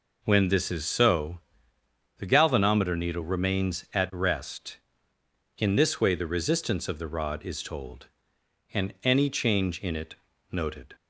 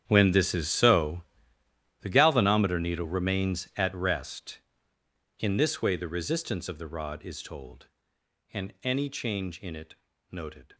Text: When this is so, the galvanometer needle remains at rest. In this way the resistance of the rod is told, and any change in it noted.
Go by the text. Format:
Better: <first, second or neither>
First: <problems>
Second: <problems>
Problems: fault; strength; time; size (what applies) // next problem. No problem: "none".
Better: first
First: pauses between "it" and "noted"; slight; at 10.1 s; 0.36 s long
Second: gets quieter; strong; throughout; 16.5 dB // pauses between "it" and "noted"; slight; at 9.9 s; 0.36 s long